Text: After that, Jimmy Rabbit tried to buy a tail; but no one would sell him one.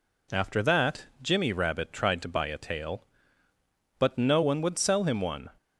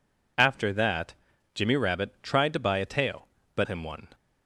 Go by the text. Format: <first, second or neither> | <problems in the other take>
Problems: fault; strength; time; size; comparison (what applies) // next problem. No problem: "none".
first | skips "no one would sell"; at 3.6 s